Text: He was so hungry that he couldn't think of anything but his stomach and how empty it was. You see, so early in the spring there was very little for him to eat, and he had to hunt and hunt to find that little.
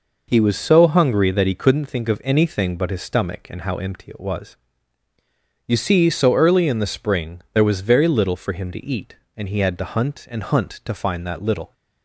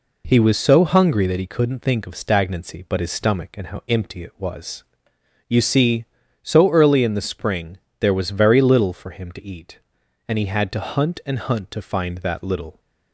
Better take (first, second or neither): first